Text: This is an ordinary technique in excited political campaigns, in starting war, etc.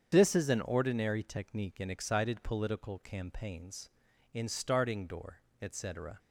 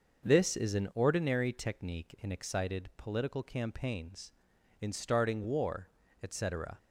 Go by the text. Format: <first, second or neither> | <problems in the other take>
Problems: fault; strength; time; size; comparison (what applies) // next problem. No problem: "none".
second | starts louder than the rest; strong; until 1.1 s; 7.5 dB; also in the second // says "door" for "war"; at 5.0 s